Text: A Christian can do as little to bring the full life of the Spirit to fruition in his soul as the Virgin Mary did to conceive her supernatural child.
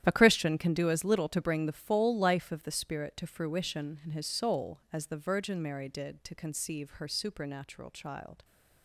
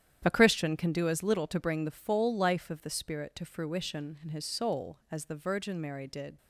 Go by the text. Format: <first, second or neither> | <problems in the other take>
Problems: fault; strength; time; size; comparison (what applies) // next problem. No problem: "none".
first | starts louder than the rest; strong; until 1.2 s; 10 dB; strong in the first // stops before "to conceive her supernatural child"; at 6.3 s